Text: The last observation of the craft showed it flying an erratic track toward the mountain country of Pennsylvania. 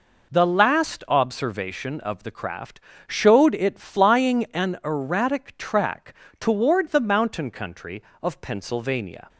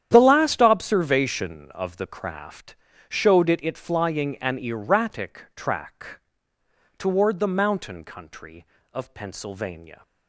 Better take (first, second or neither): first